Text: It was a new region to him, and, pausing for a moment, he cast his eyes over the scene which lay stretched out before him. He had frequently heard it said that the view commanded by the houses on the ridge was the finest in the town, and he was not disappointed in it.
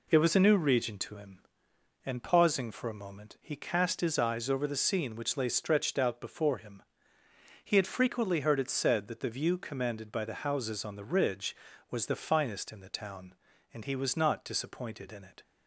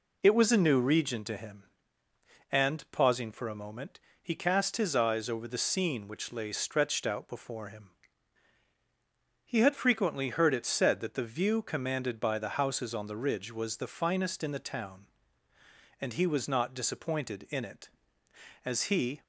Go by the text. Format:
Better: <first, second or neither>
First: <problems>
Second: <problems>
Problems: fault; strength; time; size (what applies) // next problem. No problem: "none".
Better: first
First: none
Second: goes on to say "As he"; from 18.6 s on; 0.58 s long